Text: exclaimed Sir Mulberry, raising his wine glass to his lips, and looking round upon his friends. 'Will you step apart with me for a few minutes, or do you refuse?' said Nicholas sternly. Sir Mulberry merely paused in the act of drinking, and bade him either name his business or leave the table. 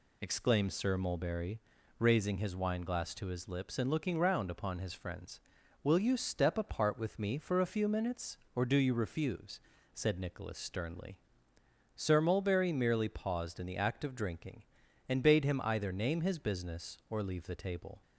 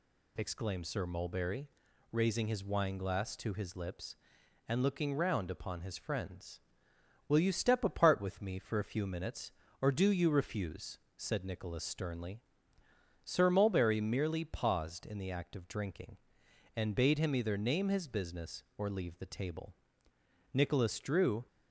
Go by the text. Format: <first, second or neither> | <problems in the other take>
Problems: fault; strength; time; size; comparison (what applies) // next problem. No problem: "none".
first | goes on to say "Nicholas drew"; noticeable; from 20.5 s on; 0.94 s long